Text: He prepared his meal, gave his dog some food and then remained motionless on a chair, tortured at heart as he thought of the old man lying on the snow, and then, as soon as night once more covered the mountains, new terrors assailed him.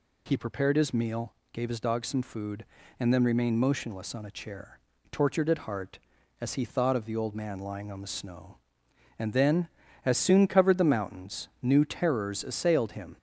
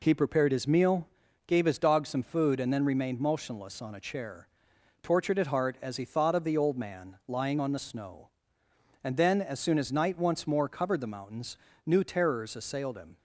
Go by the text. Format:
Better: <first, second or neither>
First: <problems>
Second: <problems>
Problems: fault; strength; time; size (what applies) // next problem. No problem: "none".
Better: second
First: skips "as night once more"; at 10.4 s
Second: none